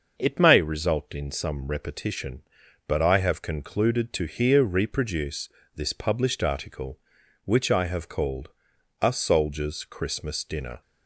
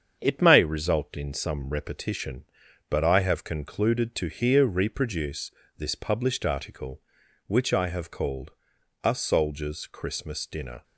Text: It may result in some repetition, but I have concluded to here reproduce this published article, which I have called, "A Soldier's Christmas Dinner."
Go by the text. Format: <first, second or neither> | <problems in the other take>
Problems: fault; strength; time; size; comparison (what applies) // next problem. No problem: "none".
first | gets quieter; throughout; 4 dB // starts louder than the rest; strong; until 1.2 s; 7.5 dB; also in the first // pauses between "reproduce" and "this"; slight; at 5.5 s; 0.26 s long; slight in the first